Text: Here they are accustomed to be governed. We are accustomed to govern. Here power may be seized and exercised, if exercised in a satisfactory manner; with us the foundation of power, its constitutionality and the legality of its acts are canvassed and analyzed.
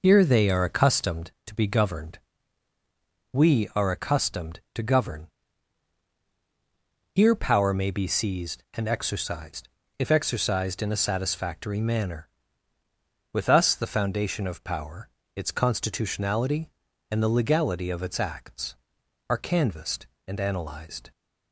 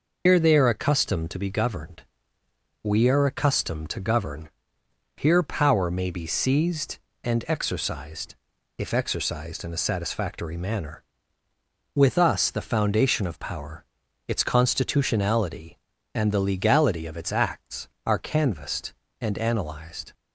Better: first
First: none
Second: loses the start of "Here"; at 0.2 s; 115 ms

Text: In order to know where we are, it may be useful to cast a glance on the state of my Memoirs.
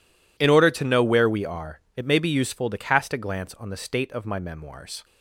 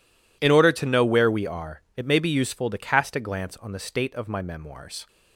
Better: neither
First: none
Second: none

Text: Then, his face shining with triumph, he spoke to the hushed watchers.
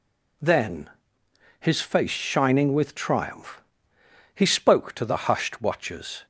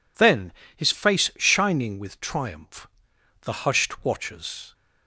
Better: first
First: none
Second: skips "he spoke to"; at 3.1 s

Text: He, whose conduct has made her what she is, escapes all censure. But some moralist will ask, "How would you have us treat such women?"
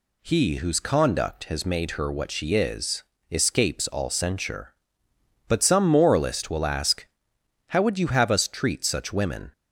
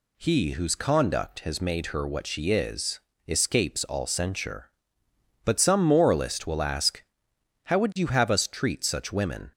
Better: neither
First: none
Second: none

